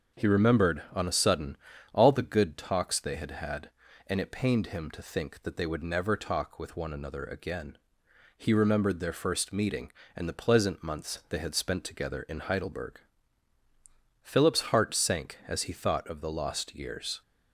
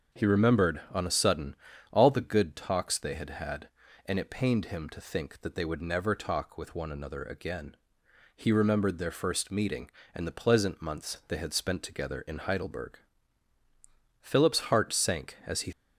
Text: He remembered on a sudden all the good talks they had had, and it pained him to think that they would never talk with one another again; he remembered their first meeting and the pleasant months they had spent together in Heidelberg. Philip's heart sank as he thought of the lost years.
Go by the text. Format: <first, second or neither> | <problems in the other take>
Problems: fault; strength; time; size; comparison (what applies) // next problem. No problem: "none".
first | starts louder than the rest; until 1.2 s; 6 dB; also in the first // pauses between "sudden" and "all"; slight; at 1.5 s; 0.34 s long; slight in the first // stops before "thought of the lost years"; at 15.7 s